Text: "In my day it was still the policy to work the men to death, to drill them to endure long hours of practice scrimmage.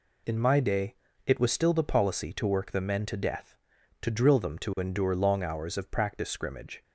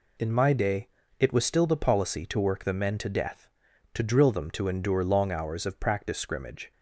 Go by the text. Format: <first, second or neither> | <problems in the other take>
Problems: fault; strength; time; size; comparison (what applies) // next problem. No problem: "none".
neither | pauses between "day" and "it"; slight; the same in both